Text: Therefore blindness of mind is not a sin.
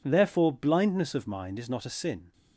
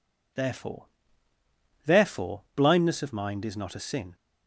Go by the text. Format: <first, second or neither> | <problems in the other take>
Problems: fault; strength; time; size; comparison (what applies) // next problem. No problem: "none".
first | says "Therefore" twice; at 1.8 s